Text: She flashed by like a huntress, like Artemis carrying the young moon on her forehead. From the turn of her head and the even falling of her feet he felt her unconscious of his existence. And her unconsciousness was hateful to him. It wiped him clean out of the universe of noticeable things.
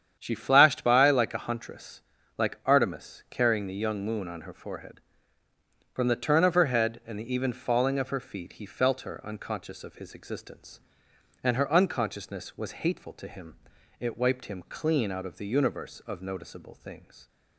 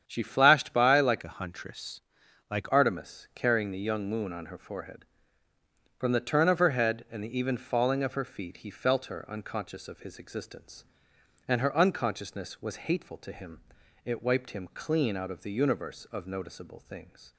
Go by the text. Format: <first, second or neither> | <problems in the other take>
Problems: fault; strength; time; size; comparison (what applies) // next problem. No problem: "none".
first | starts louder than the rest; strong; until 1.0 s; 9 dB; strong in the first // changes voice from "a" to "like"; from 1.2 to 2.7 s; 1.5 s long